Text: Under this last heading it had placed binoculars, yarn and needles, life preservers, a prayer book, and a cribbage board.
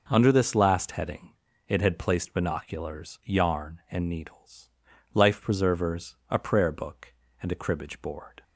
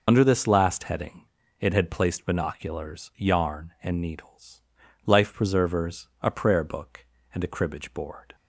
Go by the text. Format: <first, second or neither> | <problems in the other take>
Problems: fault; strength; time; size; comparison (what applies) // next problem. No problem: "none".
first | loses the start of "Under"; at 0.0 s; 95 ms // pauses between "heading" and "it"; slight; at 1.2 s; 0.34 s long; slight in the first